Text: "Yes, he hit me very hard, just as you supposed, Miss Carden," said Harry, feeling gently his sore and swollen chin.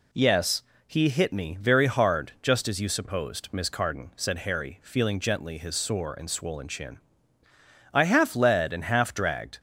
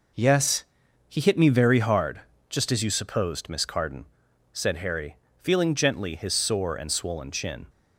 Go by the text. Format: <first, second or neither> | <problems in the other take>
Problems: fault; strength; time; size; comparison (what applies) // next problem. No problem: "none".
second | goes on to say "I half led and half dragged"; from 7.9 s on; 1.6 s long